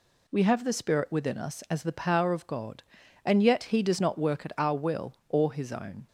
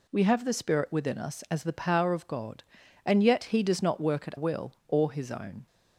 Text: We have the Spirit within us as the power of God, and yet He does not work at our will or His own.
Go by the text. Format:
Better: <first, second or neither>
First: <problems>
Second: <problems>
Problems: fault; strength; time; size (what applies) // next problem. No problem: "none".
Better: first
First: none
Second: skips "our"; at 4.3 s